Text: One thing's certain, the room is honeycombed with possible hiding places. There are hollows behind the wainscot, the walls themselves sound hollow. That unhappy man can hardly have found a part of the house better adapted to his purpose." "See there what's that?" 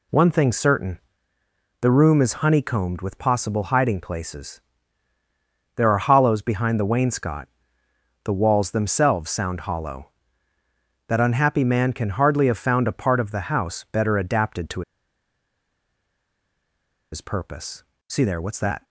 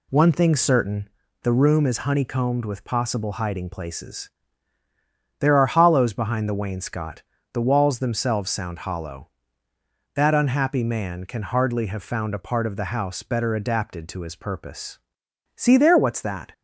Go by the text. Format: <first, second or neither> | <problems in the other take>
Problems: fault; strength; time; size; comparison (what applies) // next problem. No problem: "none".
second | pauses between "to" and "his"; strong; at 14.8 s; 2.3 s long